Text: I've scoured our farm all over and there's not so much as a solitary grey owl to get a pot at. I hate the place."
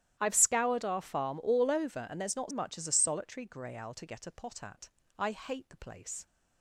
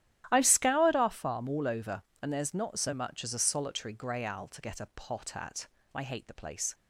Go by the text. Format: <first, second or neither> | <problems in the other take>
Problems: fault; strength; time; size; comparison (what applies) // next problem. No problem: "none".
second | starts louder than the rest; strong; until 1.2 s; 12.5 dB; strong in the second // skips "so"; at 2.5 s